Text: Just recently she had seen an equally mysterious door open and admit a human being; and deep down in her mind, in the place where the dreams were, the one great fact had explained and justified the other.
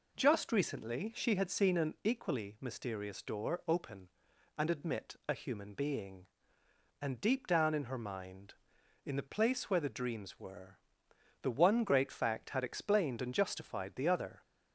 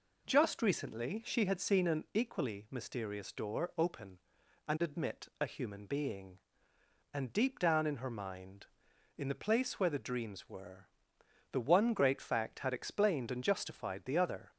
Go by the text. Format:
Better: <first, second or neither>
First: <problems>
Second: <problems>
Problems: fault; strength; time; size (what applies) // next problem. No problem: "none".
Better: neither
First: none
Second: none